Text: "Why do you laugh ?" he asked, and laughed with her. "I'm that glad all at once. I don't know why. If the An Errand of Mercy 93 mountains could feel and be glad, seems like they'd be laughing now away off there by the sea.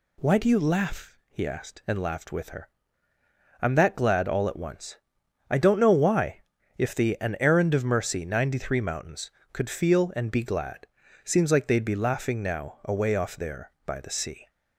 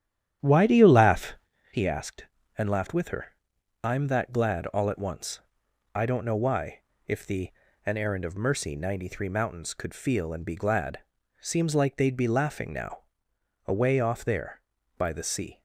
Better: first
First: none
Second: starts louder than the rest; strong; until 1.8 s; 10.5 dB // pauses between "the" and "An"; slight; at 7.5 s; 0.34 s long // pauses between "now" and "away"; noticeable; at 13.0 s; 0.62 s long

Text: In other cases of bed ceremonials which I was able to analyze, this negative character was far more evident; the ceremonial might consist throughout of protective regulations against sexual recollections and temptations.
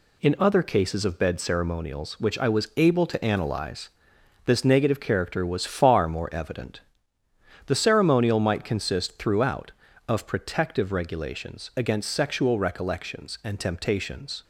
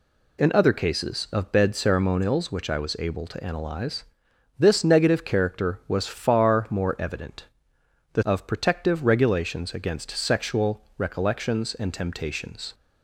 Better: first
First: none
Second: skips "ceremonial might consist throughout"; at 8.2 s

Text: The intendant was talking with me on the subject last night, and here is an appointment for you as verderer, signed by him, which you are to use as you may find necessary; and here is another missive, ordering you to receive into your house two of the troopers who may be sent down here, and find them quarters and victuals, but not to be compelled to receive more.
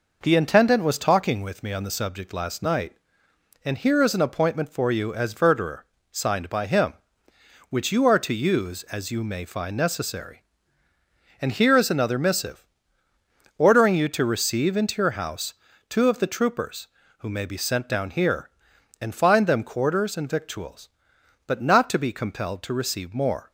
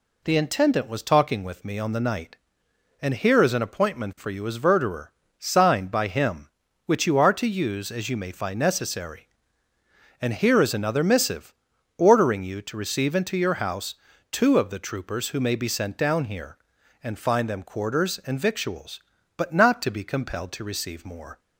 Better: first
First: pauses between "house" and "two"; slight; at 15.5 s; 0.36 s long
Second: skips "subject last"; at 2.0 s // pauses between "house" and "two"; at 13.9 s; 0.38 s long

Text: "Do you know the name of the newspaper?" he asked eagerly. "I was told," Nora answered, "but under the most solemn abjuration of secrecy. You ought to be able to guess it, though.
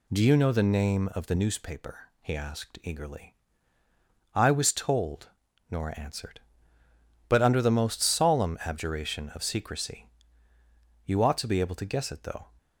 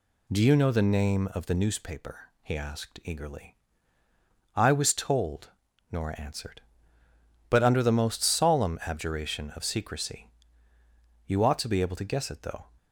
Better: neither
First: none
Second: none

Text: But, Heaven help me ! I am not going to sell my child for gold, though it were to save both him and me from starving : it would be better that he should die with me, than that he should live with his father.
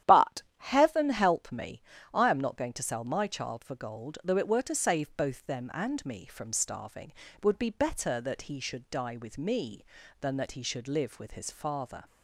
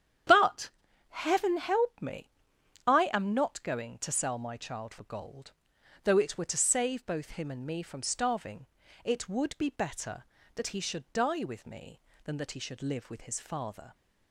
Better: second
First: starts louder than the rest; strong; until 1.2 s; 11 dB // says "them" for "him"; at 5.4 s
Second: starts louder than the rest; strong; until 1.6 s; 9.5 dB

